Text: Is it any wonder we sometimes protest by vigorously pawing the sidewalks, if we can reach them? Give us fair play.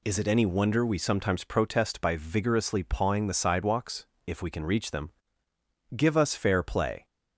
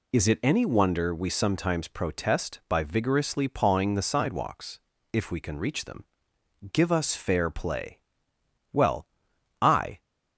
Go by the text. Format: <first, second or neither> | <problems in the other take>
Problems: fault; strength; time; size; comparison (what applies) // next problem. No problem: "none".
first | goes on to say "Well I"; noticeable; from 8.7 s on; 1.2 s long